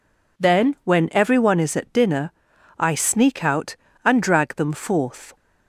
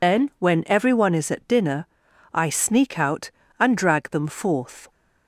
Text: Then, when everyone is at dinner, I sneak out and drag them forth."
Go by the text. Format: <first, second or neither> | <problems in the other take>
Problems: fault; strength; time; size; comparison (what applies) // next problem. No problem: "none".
first | loses the start of "Then"; at 0.0 s; 100 ms